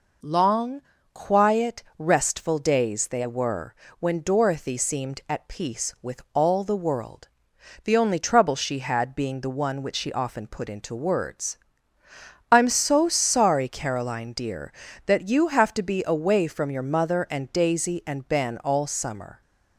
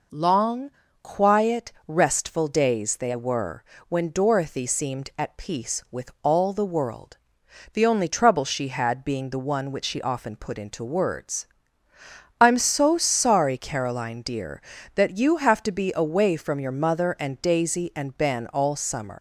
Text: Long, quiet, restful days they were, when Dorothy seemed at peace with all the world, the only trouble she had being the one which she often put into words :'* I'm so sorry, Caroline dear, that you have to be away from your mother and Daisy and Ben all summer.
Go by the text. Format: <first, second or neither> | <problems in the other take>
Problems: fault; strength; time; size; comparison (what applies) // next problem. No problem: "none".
first | leaves "summer" unfinished; at 19.1 s; 110 ms